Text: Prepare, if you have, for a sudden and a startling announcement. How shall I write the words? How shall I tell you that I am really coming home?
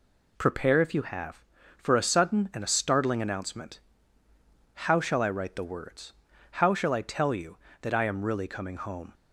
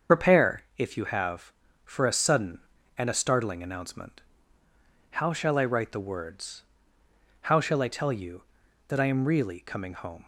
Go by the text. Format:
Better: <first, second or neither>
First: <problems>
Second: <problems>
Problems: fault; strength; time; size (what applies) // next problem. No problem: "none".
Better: first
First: none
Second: loses the start of "Prepare"; at 0.0 s; 65 ms // starts louder than the rest; until 1.2 s; 7 dB